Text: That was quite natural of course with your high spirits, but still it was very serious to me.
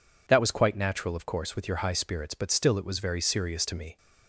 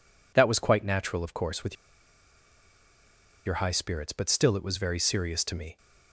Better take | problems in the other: first | pauses between "with" and "your"; strong; at 1.7 s; 1.7 s long

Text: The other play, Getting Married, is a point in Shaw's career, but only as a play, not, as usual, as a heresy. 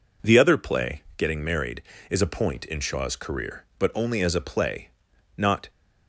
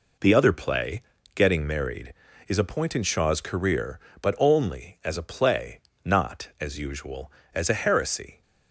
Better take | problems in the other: second | stops before "as usual as a heresy"; at 5.7 s

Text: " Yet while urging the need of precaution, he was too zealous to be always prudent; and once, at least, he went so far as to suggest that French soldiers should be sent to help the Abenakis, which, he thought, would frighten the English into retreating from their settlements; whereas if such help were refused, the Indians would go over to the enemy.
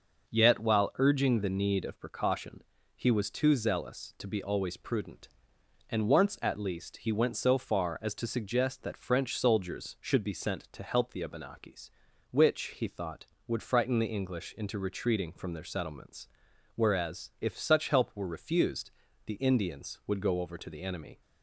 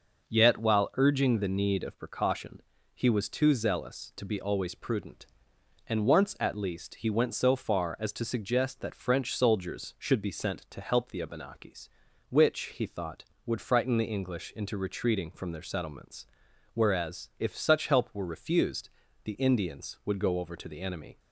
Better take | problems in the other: neither | none

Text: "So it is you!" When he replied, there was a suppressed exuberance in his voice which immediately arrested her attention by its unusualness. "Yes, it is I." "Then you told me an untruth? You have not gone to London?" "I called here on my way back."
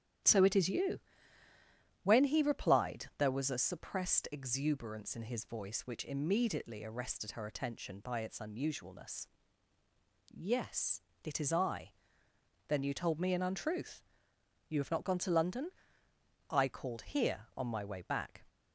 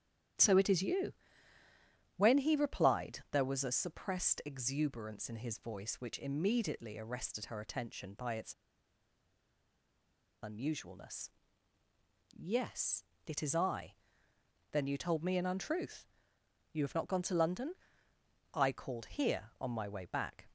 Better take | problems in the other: first | starts louder than the rest; strong; until 2.4 s; 11 dB; strong in the first // pauses between "its" and "unusualness"; strong; at 8.5 s; 1.8 s long

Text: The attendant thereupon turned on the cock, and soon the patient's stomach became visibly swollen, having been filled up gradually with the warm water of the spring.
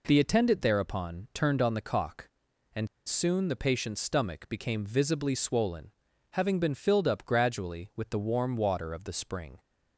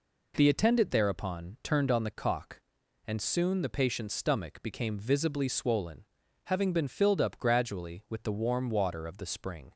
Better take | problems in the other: second | pauses between "and" and "soon"; slight; at 2.8 s; 0.18 s long

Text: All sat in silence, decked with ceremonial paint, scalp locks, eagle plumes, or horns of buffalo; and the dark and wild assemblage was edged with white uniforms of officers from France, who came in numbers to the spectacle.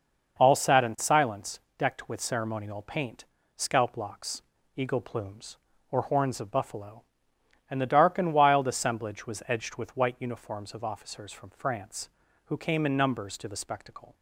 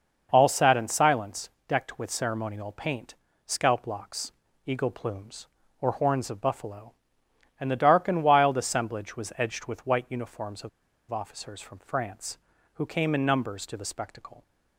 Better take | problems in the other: first | pauses between "of" and "officers"; at 10.6 s; 0.41 s long

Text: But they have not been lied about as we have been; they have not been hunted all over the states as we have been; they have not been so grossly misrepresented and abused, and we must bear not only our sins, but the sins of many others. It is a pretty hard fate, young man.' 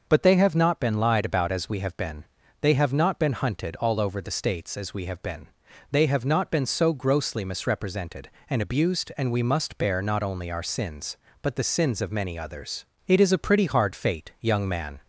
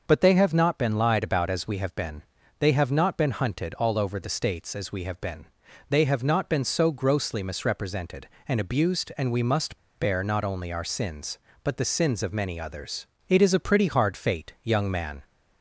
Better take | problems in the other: first | starts louder than the rest; noticeable; until 1.0 s; 6 dB; noticeable in the first // pauses between "must" and "bear"; slight; at 9.7 s; 0.23 s long

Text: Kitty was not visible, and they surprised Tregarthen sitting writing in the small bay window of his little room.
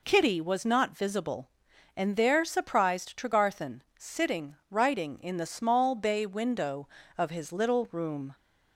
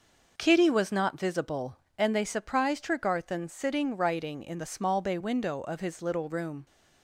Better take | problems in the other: second | says "there" for "they"; at 2.1 s // pauses between "Tregarthen" and "sitting"; slight; at 3.8 s; 0.16 s long

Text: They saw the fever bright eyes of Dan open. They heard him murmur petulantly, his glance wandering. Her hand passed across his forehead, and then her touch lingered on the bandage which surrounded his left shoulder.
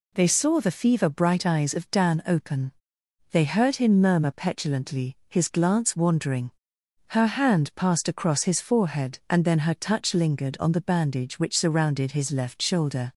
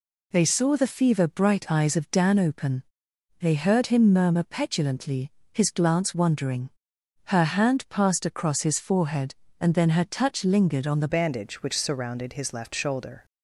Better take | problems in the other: first | changes voice at "bandage"; from 11.0 s on; 2.2 s long

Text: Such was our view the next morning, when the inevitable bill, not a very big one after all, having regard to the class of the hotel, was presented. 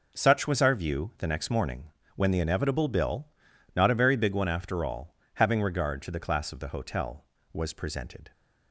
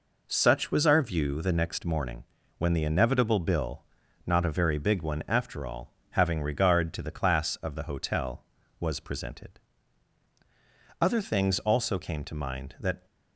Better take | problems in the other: first | goes on to say "Other things also came to mind that"; strong; from 11.0 s on; 2.0 s long

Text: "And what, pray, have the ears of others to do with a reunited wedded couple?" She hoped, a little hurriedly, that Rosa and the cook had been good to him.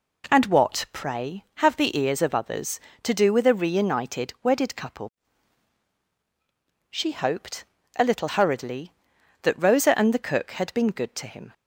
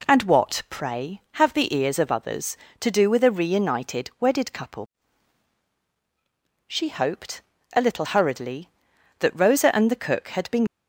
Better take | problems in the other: first | stops before "good to him"; at 10.6 s

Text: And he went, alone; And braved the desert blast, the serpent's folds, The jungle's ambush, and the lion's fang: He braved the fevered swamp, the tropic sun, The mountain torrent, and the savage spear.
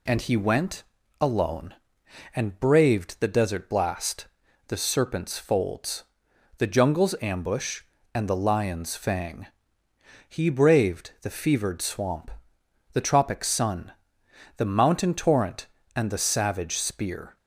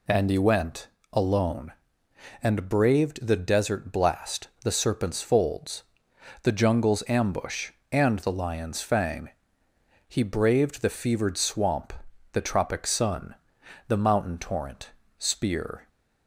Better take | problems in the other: first | skips "and the savage"; at 15.0 s

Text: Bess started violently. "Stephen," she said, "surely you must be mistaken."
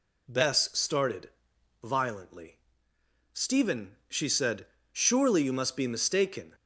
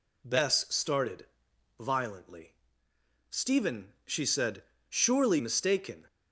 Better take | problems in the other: first | pauses between "started" and "violently"; noticeable; at 1.2 s; 0.52 s long; noticeable in the first // skips "you must be"; at 5.3 s

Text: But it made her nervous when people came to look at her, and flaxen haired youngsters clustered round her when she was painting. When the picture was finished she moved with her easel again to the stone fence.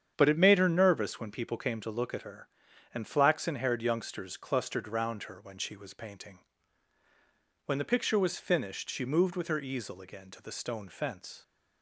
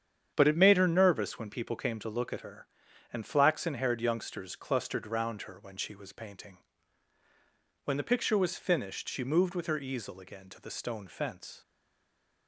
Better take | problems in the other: first | starts louder than the rest; strong; until 1.3 s; 8.5 dB; strong in the first // stays silent after the last word; slight; from 11.6 s on; 0.8 s long

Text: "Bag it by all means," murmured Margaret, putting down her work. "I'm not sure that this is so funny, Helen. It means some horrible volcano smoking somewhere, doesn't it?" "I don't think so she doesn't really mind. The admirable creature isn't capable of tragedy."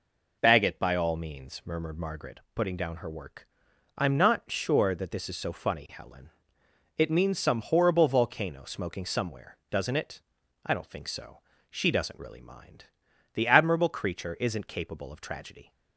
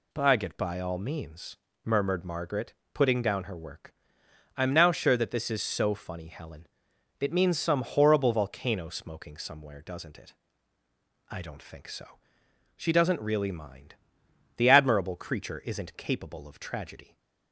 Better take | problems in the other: first | says "now" for "not"; at 4.7 s // pauses between "so" and "she"; noticeable; at 12.1 s; 0.60 s long; slight in the first

